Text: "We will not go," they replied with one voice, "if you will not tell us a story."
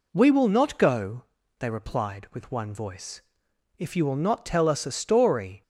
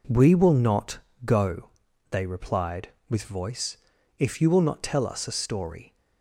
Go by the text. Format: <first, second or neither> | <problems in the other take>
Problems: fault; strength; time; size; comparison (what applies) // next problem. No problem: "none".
first | pauses between "not" and "go"; slight; at 0.9 s; 0.24 s long // skips "one"; at 3.2 s